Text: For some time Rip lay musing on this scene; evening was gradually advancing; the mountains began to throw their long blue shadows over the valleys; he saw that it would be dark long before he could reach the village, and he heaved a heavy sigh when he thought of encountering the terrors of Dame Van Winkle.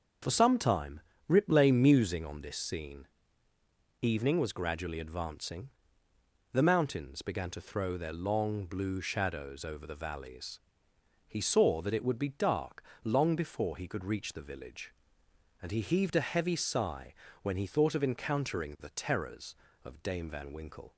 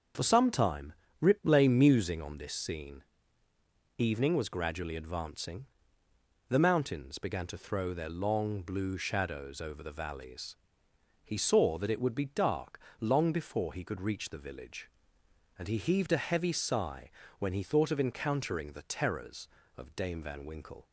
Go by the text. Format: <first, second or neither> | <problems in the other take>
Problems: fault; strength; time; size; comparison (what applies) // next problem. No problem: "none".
neither | starts louder than the rest; the same in both // pauses between "time" and "Rip"; slight; the same in both // pauses between "dark" and "long"; slight; the same in both // pauses between "sigh" and "when"; slight; the same in both